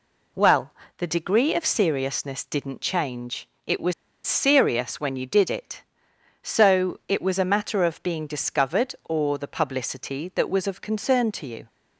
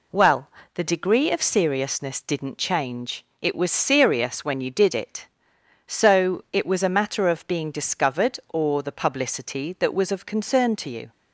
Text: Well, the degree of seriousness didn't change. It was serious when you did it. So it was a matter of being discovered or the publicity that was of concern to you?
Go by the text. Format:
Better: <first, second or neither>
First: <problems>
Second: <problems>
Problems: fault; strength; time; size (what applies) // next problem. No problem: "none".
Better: second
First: pauses between "was" and "serious"; slight; at 3.9 s; 0.33 s long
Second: none